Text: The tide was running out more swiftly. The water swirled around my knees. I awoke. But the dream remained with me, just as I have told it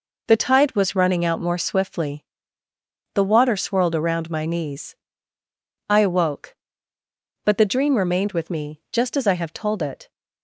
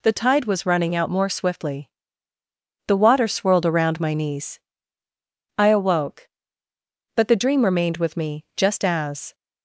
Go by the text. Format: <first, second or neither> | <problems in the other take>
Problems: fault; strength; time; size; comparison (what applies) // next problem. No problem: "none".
first | stops before "I have told it"; at 9.3 s